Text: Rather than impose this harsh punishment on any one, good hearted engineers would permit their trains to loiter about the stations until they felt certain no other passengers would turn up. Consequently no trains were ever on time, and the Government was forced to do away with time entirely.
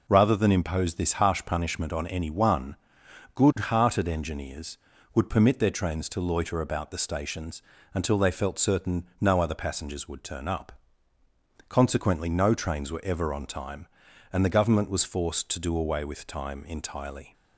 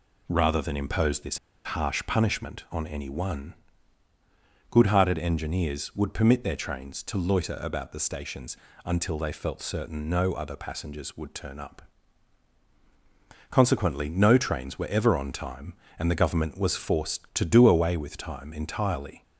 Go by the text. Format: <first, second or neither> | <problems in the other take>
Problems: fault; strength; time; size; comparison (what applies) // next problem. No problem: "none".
first | pauses between "this" and "harsh"; slight; at 1.3 s; 0.27 s long // pauses between "stations" and "until"; slight; at 8.5 s; 0.28 s long; slight in the first